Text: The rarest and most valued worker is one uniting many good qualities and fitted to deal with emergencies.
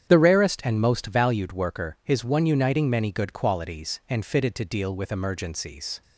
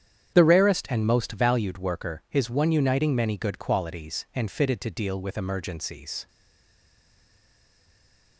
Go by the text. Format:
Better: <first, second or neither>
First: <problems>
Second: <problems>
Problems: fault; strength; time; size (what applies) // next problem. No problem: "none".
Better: first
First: starts louder than the rest; strong; until 1.1 s; 9 dB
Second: starts louder than the rest; strong; until 1.3 s; 9 dB // stays silent after the last word; from 6.2 s on; 2.1 s long